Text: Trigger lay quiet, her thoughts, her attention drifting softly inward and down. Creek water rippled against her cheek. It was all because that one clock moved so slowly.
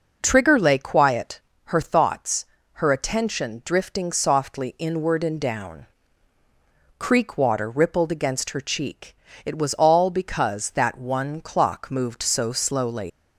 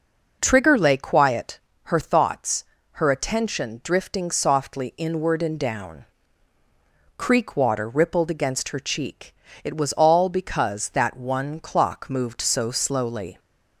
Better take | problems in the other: second | leaves "slowly" unfinished; at 13.0 s; 100 ms

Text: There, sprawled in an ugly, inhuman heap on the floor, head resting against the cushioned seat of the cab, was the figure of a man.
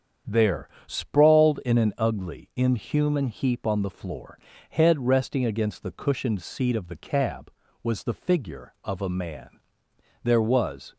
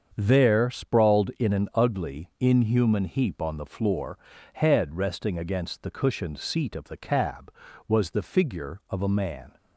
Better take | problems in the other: second | starts louder than the rest; strong; until 1.4 s; 8 dB; also in the second // goes on to say "There was"; noticeable; from 10.2 s on; 0.72 s long

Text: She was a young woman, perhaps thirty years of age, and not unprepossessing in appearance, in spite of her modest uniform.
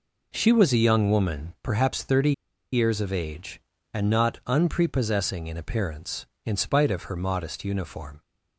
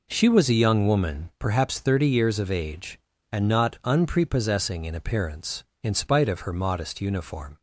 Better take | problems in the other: second | pauses between "thirty" and "years"; at 2.3 s; 0.40 s long

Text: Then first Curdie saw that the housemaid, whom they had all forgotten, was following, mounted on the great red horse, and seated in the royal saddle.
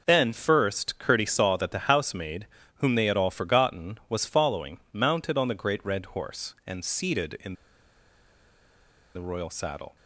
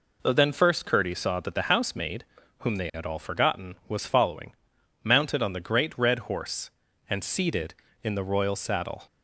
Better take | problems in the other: second | pauses between "in" and "the"; strong; at 7.5 s; 1.6 s long

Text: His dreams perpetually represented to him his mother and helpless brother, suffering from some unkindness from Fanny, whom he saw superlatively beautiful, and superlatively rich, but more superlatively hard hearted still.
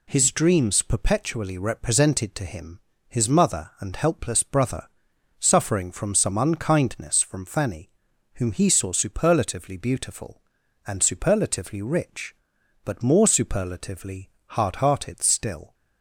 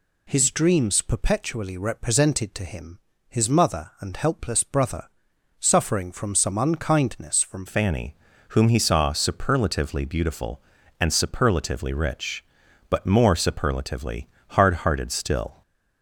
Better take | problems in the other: first | pauses between "him" and "his"; slight; at 3.0 s; 0.30 s long; slight in the first // changes voice at "Fanny"; from 7.6 s on; 8.0 s long // pauses between "superlatively" and "hard"; slight; at 14.2 s; 0.22 s long; slight in the first

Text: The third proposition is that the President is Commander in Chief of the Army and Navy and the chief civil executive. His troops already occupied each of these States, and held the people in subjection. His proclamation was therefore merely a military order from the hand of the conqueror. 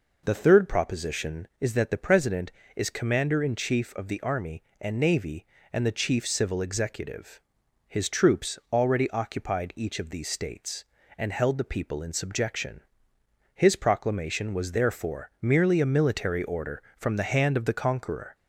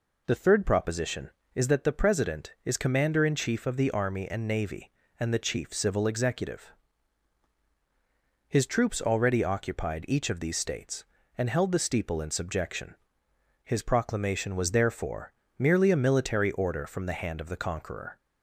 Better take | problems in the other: first | says "steeple" for "people"; at 11.7 s // pauses between "therefore" and "merely"; slight; at 15.3 s; 0.26 s long

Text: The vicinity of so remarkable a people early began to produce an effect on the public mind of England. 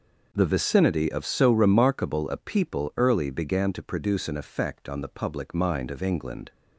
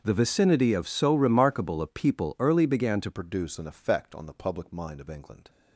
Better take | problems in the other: first | starts louder than the rest; until 1.0 s; 6.5 dB // changes voice at "produce"; from 3.1 s on; 2.3 s long

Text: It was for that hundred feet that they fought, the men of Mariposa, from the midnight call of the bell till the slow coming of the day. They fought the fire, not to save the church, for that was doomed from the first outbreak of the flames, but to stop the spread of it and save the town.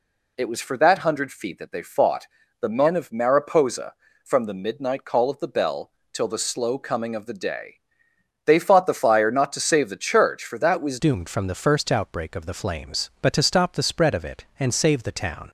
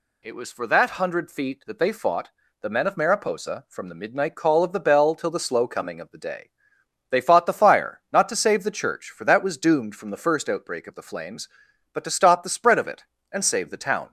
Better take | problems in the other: second | pauses between "bell" and "till"; slight; at 5.9 s; 0.22 s long // changes voice at "doomed"; from 10.9 s on; 4.5 s long

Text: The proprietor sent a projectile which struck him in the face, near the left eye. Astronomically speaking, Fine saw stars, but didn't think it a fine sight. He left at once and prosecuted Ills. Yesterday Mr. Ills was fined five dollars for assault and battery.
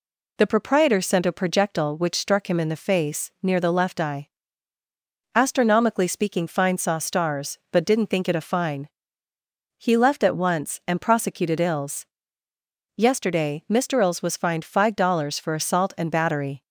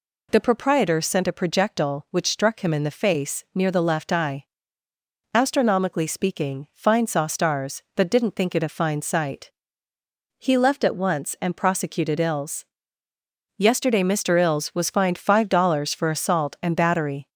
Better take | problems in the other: second | skips "sight"; at 9.3 s

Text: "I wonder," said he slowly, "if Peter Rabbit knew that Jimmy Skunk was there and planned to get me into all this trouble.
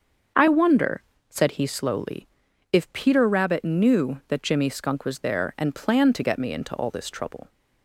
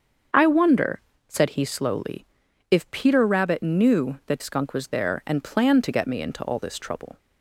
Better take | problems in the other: first | starts louder than the rest; until 1.6 s; 7 dB; also in the first // skips "Jimmy"; at 4.4 s

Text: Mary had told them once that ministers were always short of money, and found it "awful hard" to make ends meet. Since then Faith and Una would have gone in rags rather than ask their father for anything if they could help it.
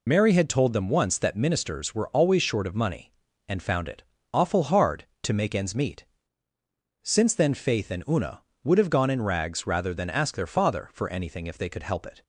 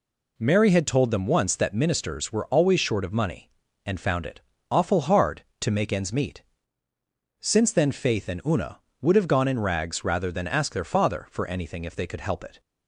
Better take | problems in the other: second | loses the start of "Mary"; at 0.0 s; 65 ms // pauses between "it" and "awful"; slight; at 4.0 s; 0.28 s long; slight in the second

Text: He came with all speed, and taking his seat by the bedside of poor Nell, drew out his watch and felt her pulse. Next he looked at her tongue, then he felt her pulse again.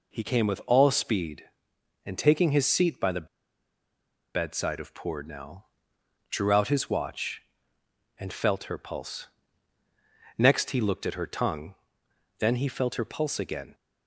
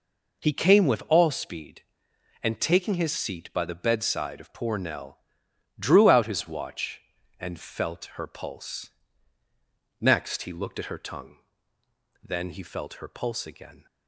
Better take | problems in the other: second | pauses between "the" and "bedside"; at 3.2 s; 1.0 s long

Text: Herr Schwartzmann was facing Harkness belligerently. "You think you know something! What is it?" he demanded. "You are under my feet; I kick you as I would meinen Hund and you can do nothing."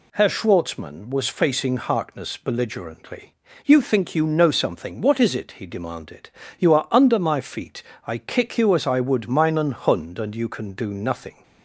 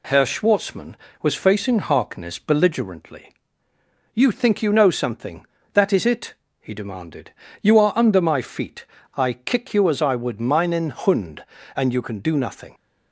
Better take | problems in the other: first | says "That" for "What"; at 5.7 s

